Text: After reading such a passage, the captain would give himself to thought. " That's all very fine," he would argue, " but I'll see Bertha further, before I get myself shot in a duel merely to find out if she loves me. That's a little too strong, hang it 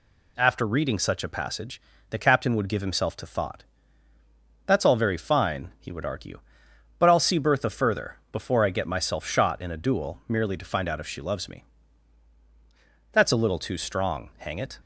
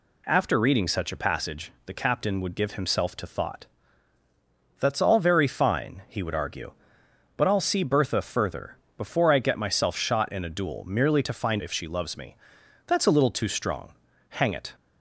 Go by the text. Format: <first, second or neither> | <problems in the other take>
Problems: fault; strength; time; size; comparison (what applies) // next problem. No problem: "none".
first | skips "out"; at 11.6 s